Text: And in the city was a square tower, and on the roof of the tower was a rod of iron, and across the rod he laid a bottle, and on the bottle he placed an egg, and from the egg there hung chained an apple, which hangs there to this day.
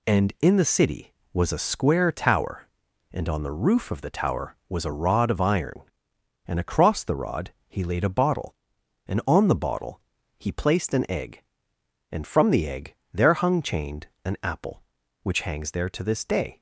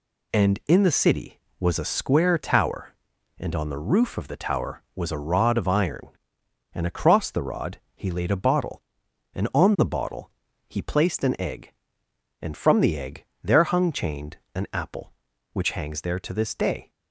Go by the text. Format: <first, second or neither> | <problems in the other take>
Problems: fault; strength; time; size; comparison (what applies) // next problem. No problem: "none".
neither | pauses between "rod" and "he"; slight; the same in both // pauses between "bottle" and "he"; slight; the same in both // pauses between "egg" and "there"; slight; the same in both // pauses between "chained" and "an"; slight; the same in both